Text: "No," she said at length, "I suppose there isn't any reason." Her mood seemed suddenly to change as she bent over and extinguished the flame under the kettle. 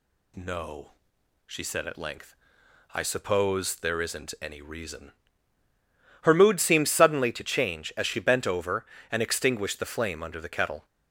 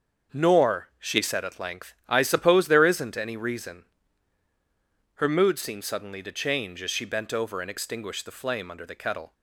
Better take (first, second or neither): first